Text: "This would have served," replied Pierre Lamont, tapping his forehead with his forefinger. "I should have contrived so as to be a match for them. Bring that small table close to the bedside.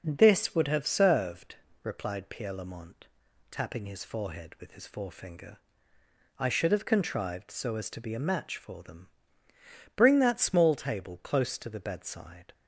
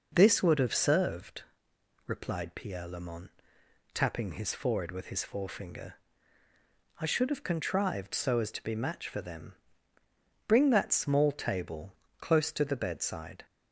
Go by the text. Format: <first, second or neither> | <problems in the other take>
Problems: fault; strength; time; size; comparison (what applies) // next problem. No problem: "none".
first | skips "a"; at 8.7 s // pauses between "table" and "close"; slight; at 11.9 s; 0.24 s long